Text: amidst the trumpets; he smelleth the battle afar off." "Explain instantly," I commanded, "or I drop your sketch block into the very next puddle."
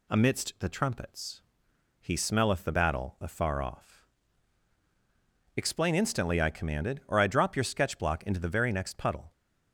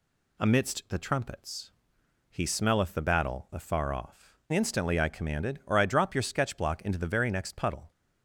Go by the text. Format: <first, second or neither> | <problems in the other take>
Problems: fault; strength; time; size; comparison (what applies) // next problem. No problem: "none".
first | skips "Explain"; at 4.4 s